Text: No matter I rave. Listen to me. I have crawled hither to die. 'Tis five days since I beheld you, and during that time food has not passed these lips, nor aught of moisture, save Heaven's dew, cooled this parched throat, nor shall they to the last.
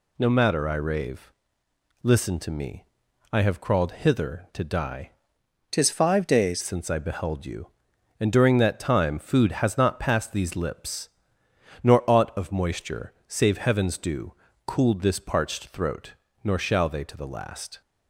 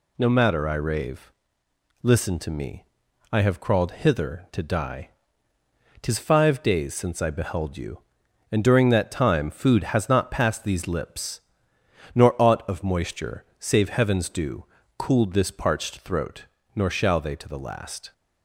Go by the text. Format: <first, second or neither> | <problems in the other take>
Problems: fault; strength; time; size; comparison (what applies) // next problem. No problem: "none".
second | changes voice from "Tis" to "days"; from 5.7 to 6.6 s; 0.9 s long